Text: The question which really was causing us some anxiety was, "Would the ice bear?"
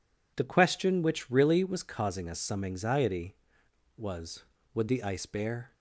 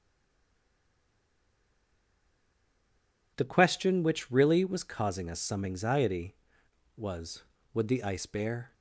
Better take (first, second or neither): first